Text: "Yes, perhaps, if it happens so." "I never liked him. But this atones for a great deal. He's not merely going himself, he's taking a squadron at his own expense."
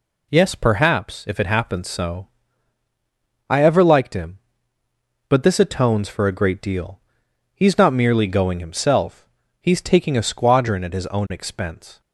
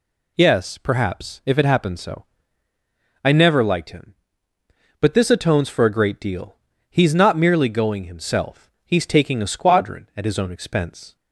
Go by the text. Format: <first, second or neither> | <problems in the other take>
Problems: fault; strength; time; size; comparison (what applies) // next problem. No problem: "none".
second | says "ever" for "never"; at 3.6 s